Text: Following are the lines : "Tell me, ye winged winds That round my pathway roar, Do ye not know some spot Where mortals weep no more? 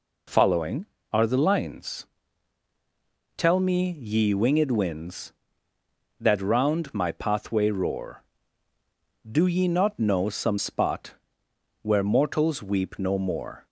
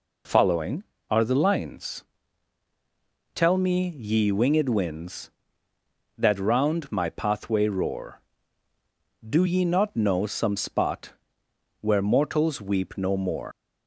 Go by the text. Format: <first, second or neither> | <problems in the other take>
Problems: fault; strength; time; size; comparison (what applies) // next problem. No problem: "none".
first | pauses between "spot" and "Where"; noticeable; at 11.1 s; 0.68 s long; noticeable in the first // leaves "more" unfinished; at 13.5 s; 140 ms